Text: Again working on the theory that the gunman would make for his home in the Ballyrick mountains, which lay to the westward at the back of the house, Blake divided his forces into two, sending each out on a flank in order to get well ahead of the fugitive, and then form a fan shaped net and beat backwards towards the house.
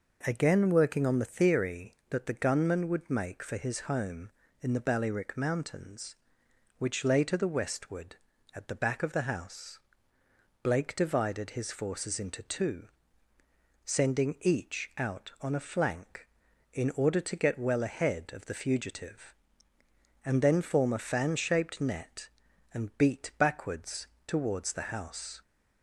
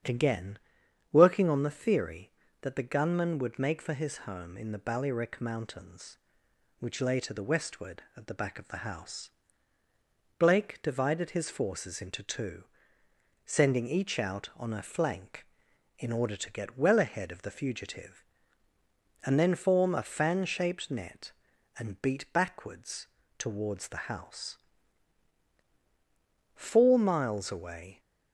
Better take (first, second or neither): first